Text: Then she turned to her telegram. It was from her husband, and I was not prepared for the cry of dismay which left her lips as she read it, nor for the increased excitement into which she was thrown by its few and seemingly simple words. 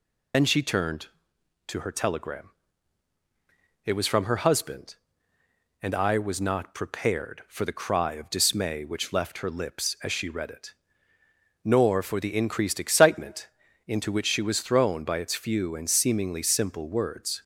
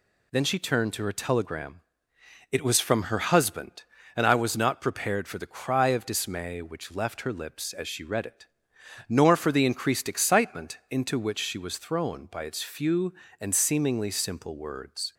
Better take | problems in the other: second | loses the start of "Then"; at 0.3 s; 60 ms // pauses between "excitement" and "into"; slight; at 13.4 s; 0.36 s long

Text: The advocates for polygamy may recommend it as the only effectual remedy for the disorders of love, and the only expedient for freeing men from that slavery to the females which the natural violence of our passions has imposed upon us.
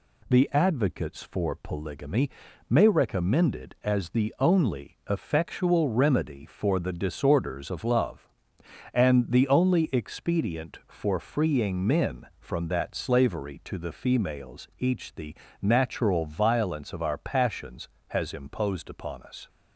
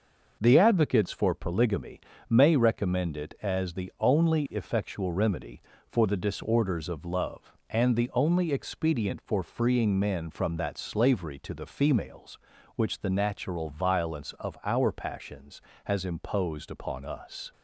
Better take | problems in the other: second | pauses between "polygamy" and "may"; at 2.2 s; 0.40 s long; slight in the second // says "each" for "which"; at 14.7 s // pauses between "the" and "natural"; slight; at 15.3 s; 0.26 s long

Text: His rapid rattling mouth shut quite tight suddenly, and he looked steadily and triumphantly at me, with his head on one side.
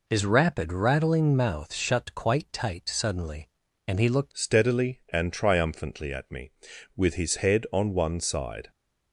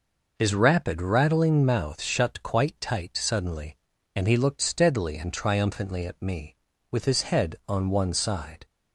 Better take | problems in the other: second | changes voice at "steadily"; from 4.3 s on; 4.4 s long

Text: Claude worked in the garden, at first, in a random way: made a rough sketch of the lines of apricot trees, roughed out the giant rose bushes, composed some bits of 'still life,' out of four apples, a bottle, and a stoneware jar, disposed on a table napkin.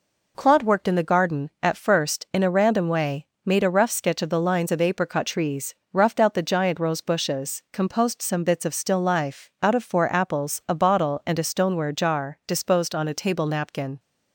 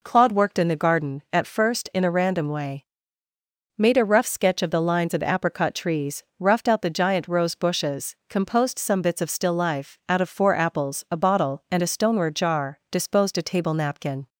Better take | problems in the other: first | skips "on"; at 13.3 s

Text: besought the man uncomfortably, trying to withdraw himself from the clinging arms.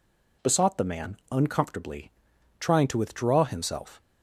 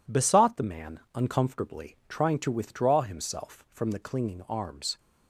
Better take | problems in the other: second | pauses between "man" and "uncomfortably"; slight; at 1.1 s; 0.16 s long; slight in the second // stops before "from the clinging arms"; at 4.0 s

